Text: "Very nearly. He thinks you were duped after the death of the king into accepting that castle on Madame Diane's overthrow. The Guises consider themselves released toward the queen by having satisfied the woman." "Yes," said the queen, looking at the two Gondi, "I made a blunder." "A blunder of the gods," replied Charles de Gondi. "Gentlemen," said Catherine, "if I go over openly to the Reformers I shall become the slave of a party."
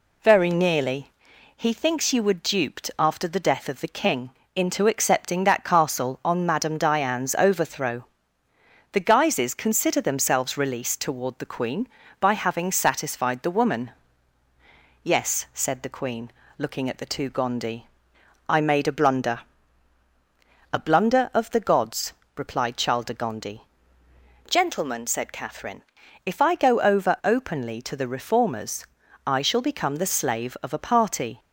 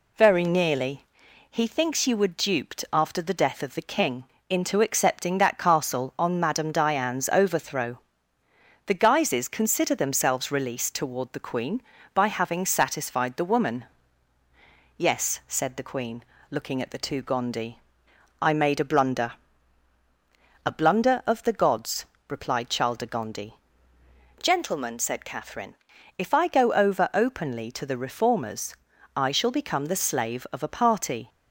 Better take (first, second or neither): neither